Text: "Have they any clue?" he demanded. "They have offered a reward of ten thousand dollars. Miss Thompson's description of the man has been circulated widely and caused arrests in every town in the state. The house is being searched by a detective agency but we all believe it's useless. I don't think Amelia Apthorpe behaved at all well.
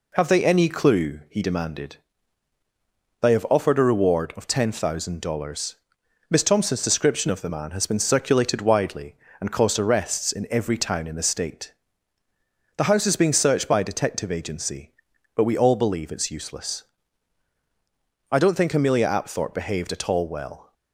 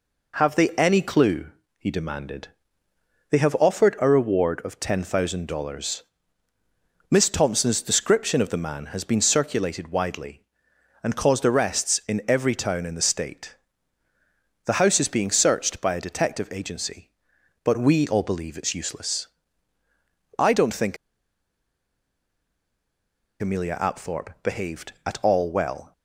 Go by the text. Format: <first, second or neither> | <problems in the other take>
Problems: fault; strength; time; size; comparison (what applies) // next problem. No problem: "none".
first | pauses between "think" and "Amelia"; strong; at 20.9 s; 2.4 s long